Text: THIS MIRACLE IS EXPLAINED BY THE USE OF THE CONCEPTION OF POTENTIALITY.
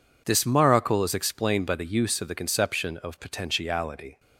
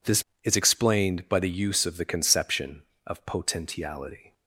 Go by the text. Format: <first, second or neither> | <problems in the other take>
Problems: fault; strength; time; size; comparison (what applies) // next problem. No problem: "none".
first | skips "MIRACLE"; at 0.3 s